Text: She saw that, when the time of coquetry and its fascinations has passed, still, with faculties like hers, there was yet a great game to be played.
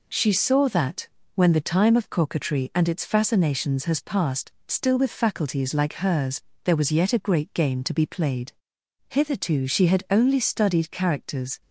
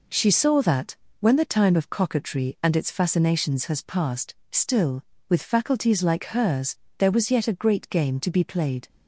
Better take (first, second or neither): second